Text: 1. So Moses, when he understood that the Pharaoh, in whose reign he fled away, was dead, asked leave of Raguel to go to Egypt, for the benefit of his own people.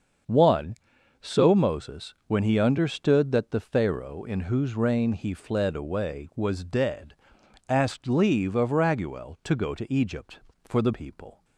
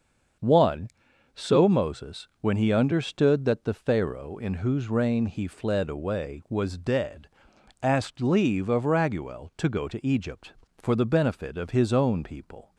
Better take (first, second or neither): second